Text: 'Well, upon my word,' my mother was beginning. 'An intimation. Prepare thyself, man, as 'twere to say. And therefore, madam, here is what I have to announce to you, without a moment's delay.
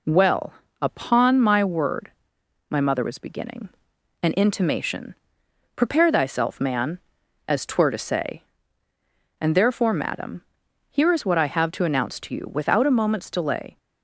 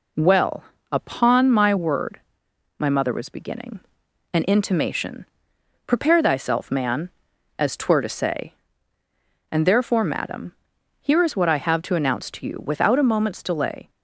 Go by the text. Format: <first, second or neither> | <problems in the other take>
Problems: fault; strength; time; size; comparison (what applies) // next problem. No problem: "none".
neither | none